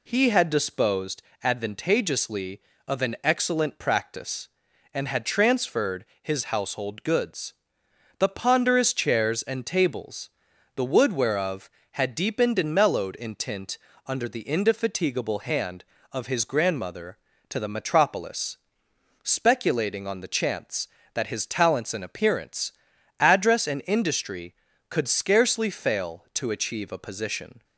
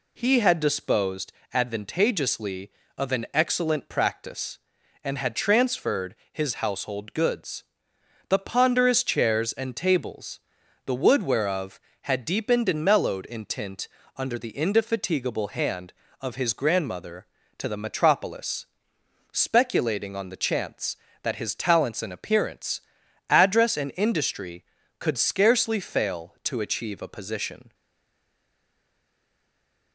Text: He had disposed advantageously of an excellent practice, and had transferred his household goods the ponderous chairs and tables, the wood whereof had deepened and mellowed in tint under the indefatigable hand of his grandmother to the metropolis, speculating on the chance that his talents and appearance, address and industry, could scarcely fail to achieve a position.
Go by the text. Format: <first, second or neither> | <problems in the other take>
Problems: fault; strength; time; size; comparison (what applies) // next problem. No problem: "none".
first | pauses between "disposed" and "advantageously"; slight; at 1.3 s; 0.22 s long; slight in the first // pauses between "transferred" and "his"; slight; at 6.1 s; 0.18 s long; slight in the first // pauses between "goods" and "the"; noticeable; at 7.6 s; 0.64 s long; noticeable in the first // pauses between "tint" and "under"; slight; at 13.8 s; 0.28 s long; slight in the first // stays silent after the last word; from 27.7 s on; 2.2 s long